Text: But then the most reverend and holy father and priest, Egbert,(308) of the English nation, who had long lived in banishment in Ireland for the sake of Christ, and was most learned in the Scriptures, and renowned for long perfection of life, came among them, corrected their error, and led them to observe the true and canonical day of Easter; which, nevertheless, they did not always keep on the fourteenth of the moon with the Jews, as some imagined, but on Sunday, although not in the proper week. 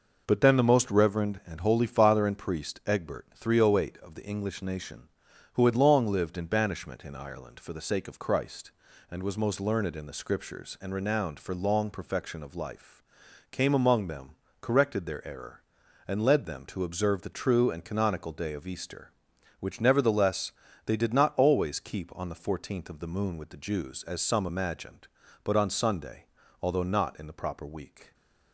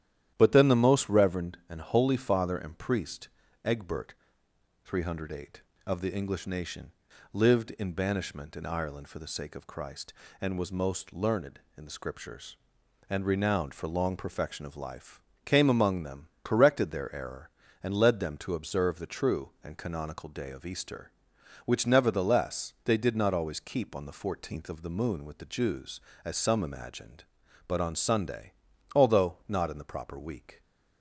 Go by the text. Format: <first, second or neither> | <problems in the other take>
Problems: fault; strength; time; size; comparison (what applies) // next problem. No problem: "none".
first | starts louder than the rest; strong; until 1.3 s; 11.5 dB // skips "who had long"; at 7.1 s